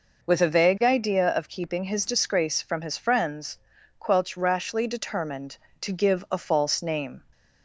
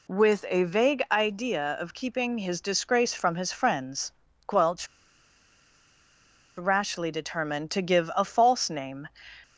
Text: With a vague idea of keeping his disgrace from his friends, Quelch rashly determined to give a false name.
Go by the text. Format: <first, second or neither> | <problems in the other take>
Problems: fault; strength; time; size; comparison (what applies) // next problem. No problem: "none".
first | pauses between "Quelch" and "rashly"; strong; at 4.8 s; 1.7 s long